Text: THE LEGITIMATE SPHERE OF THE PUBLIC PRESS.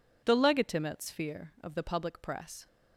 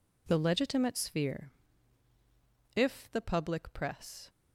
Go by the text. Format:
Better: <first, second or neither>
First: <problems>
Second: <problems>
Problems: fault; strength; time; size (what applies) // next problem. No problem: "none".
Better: first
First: none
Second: says "If" for "OF"; at 2.7 s